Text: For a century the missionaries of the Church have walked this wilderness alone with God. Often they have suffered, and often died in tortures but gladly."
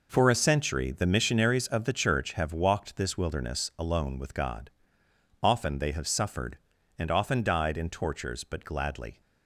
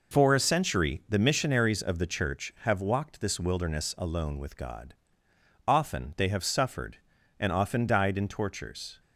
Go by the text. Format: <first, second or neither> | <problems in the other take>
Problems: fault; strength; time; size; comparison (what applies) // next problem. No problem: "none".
first | stops before "but gladly"; at 9.0 s